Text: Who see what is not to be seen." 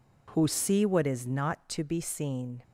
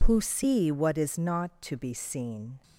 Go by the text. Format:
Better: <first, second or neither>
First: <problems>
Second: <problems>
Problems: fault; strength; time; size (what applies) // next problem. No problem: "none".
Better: neither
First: none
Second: none